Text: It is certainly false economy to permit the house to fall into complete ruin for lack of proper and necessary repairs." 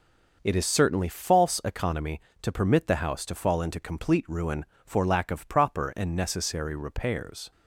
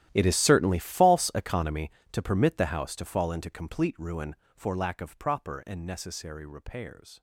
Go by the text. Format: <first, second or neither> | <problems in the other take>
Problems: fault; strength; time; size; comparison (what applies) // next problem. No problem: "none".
first | gets quieter; strong; throughout; 18.5 dB